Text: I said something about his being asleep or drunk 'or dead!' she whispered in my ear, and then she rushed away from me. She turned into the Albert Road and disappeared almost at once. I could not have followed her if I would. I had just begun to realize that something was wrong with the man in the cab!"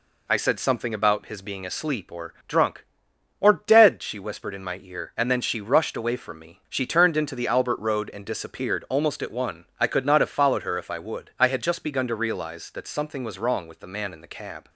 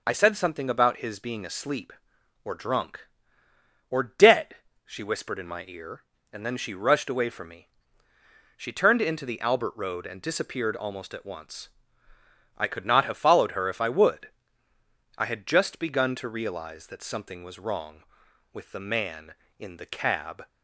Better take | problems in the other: second | says "one" for "once"; at 9.3 s

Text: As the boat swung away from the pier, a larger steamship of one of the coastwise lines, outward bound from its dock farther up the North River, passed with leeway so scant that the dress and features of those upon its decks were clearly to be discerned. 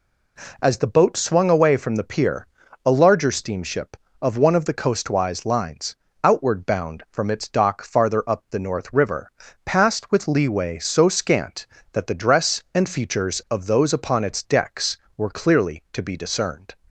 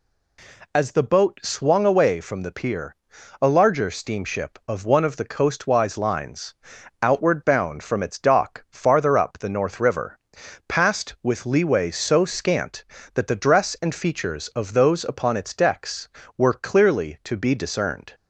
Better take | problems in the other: neither | none

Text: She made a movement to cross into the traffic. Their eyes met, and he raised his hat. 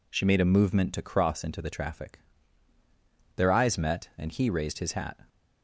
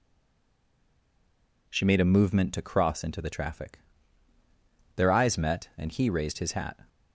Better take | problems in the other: first | stays silent before the first word; noticeable; until 1.6 s; 1.6 s long

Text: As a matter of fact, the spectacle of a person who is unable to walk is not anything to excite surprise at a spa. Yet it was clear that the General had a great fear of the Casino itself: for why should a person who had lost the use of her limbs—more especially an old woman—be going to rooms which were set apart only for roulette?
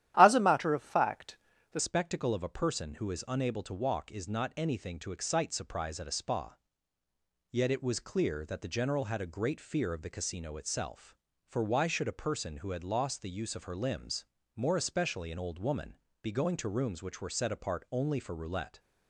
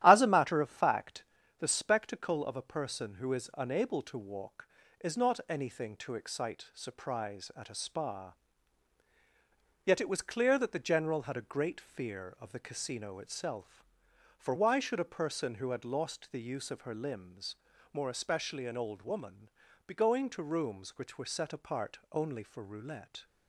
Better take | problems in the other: second | starts louder than the rest; strong; until 1.1 s; 12 dB; strong in the second // changes voice at "spectacle"; from 1.7 s on; 17.0 s long

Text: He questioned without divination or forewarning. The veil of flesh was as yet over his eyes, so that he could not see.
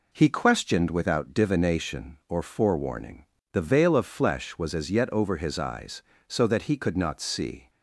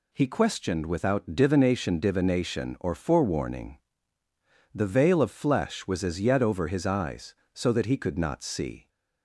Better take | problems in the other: first | says "divination" twice; at 1.9 s

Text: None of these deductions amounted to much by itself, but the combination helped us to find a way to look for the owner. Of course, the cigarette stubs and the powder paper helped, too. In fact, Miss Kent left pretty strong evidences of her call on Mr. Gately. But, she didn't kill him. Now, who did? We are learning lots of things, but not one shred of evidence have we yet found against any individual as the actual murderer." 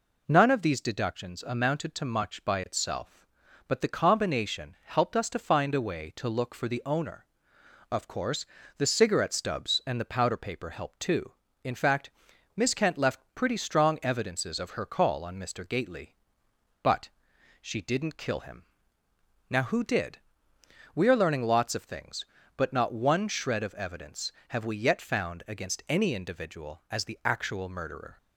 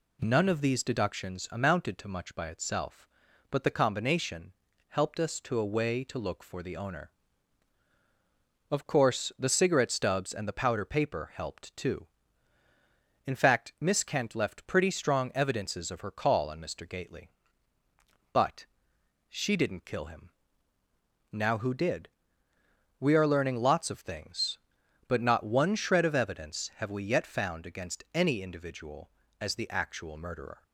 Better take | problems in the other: first | pauses between "combination" and "helped"; slight; at 4.5 s; 0.36 s long // skips "find"; at 5.5 s

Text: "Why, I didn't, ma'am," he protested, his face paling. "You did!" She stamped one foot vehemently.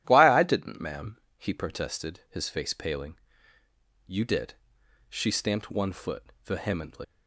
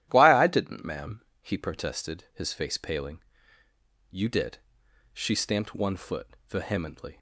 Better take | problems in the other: second | starts louder than the rest; strong; until 1.0 s; 12 dB; strong in the second // pauses between "foot" and "vehemently"; slight; at 6.2 s; 0.20 s long; slight in the second // leaves "vehemently" unfinished; at 7.0 s; 95 ms

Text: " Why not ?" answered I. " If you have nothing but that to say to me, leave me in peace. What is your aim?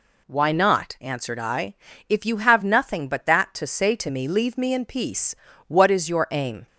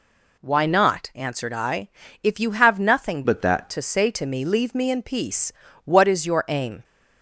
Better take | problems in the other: first | changes voice from "but" to "that"; from 3.2 to 3.7 s; 0.5 s long

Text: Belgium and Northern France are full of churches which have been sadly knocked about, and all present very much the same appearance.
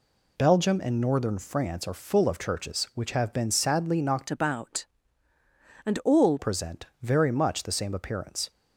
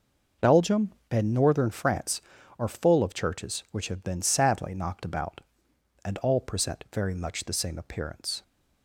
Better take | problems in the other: second | changes voice from "about" to "all"; from 4.2 to 6.3 s; 2.1 s long // pauses between "present" and "very"; slight; at 6.8 s; 0.18 s long

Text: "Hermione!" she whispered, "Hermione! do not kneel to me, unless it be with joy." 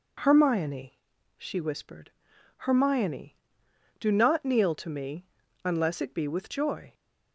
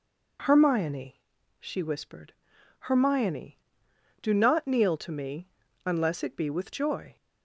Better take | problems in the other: neither | none

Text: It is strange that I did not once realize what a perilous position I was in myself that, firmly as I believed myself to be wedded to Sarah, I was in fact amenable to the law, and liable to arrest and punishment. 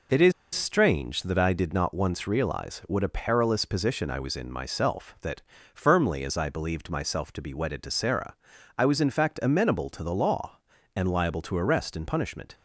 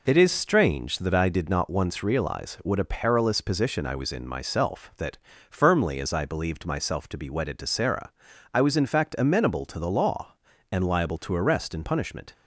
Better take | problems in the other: second | pauses between "is" and "strange"; slight; at 0.3 s; 0.22 s long

